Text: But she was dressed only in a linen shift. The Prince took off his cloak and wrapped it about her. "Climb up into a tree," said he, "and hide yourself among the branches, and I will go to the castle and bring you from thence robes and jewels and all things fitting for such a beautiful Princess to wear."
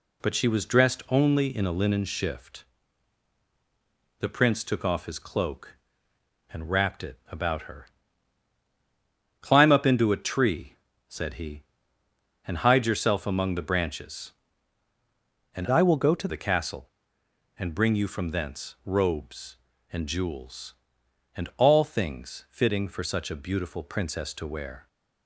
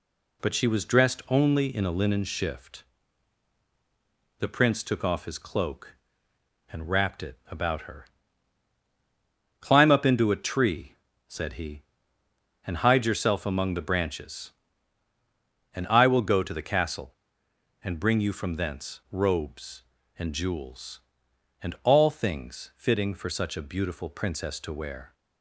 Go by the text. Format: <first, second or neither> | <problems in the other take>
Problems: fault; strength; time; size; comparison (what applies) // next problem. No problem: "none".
second | changes voice from "I" to "to"; from 15.6 to 16.2 s; 0.6 s long